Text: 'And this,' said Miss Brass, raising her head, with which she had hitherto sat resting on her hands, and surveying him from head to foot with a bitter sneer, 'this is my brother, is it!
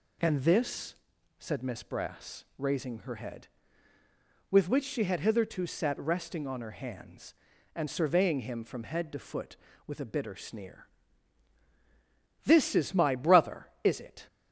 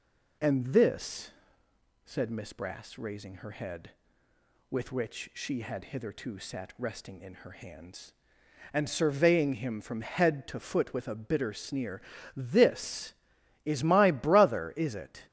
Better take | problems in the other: first | says "in" for "on"; at 7.2 s

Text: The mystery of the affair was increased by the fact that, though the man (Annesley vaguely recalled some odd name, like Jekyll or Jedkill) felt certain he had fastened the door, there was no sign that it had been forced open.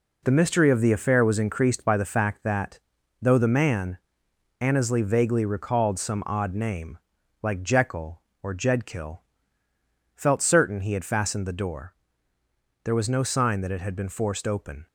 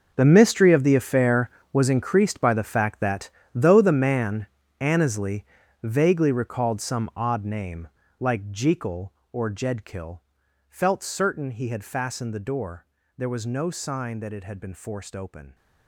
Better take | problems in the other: first | gets quieter; strong; throughout; 15 dB // pauses between "Annesley" and "vaguely"; at 5.4 s; 0.38 s long

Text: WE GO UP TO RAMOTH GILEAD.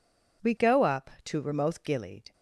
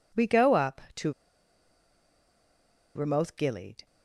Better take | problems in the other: first | pauses between "TO" and "RAMOTH"; strong; at 1.1 s; 1.8 s long

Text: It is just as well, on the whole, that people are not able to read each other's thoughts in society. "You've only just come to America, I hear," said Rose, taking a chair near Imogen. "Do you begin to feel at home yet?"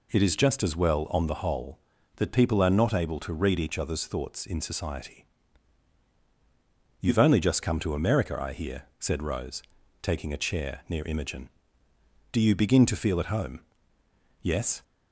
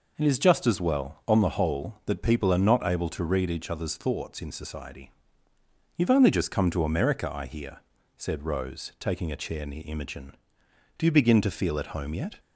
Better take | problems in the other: second | says "yes" for "yet"; at 14.4 s

